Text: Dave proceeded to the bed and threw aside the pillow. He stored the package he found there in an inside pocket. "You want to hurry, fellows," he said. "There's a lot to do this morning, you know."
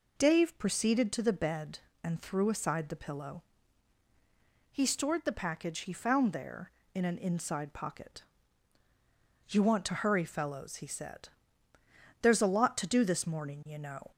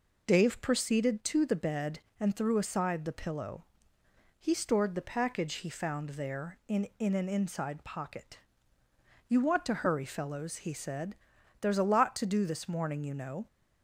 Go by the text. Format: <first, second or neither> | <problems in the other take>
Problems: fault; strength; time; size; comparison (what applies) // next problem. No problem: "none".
first | says "in" twice; at 6.9 s